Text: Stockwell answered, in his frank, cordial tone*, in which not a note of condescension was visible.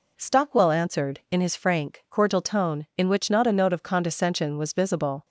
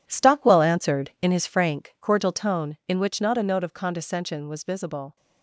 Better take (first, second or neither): first